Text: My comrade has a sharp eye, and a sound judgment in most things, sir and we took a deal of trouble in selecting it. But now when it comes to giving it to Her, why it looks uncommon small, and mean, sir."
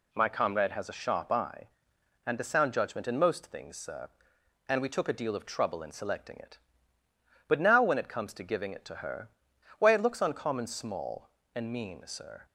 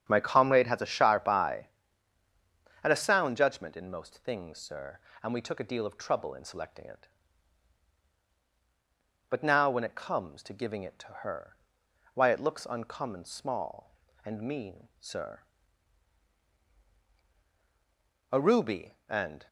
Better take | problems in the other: first | starts louder than the rest; strong; until 1.1 s; 8 dB // goes on to say "A ruby and"; noticeable; from 18.3 s on; 1.1 s long

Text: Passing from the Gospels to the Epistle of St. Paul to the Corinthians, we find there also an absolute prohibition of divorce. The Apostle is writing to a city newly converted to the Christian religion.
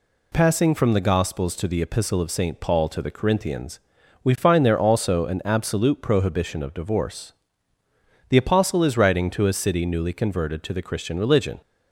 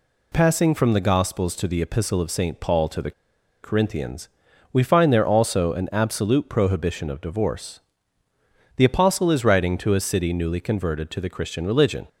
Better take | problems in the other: first | pauses between "the" and "Corinthians"; noticeable; at 3.1 s; 0.51 s long

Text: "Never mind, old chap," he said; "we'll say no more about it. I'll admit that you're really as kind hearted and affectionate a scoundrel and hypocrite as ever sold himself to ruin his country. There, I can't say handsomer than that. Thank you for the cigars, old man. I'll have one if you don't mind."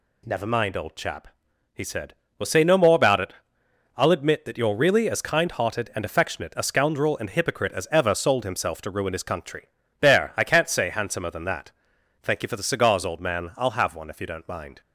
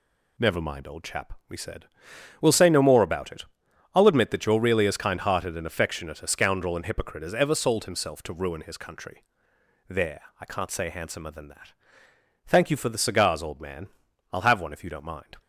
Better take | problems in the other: first | says "we" for "he"; at 1.4 s

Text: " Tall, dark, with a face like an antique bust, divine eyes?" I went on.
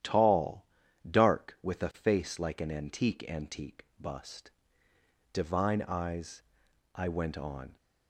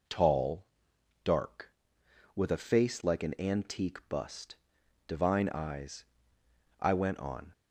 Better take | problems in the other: second | starts louder than the rest; strong; until 1.4 s; 11 dB // says "antique" twice; at 3.2 s

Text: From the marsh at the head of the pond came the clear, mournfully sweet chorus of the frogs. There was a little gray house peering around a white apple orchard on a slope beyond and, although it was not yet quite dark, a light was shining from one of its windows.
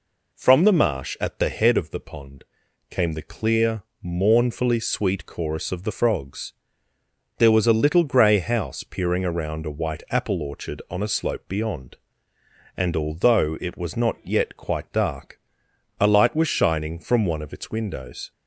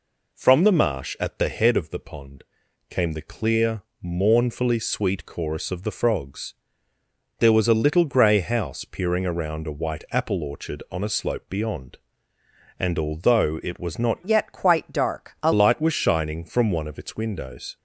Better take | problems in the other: first | pauses between "pond" and "came"; noticeable; at 2.4 s; 0.46 s long; noticeable in the first // changes voice from "yet" to "a"; from 14.2 to 15.5 s; 1.3 s long

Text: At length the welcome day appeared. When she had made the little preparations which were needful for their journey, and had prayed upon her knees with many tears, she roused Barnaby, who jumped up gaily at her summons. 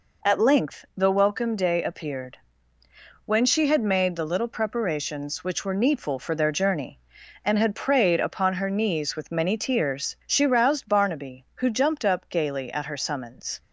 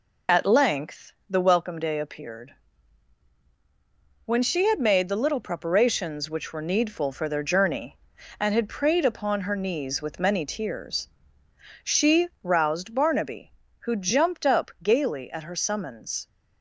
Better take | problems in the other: first | loses the start of "At"; at 0.2 s; 30 ms // pauses between "length" and "the"; slight; at 1.1 s; 0.16 s long // pauses between "she" and "roused"; slight; at 12.2 s; 0.16 s long

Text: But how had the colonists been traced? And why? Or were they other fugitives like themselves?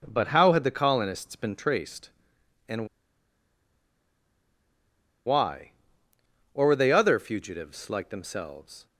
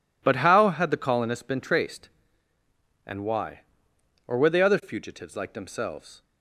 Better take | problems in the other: second | pauses between "And" and "why"; strong; at 2.8 s; 2.3 s long

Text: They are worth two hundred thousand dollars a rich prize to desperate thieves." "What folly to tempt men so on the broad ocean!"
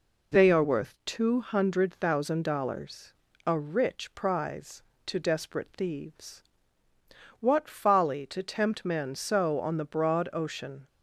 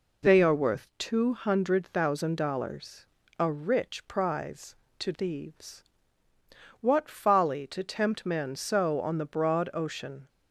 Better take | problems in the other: first | pauses between "dollars" and "a"; slight; at 3.0 s; 0.34 s long; slight in the first // skips "desperate"; at 5.1 s

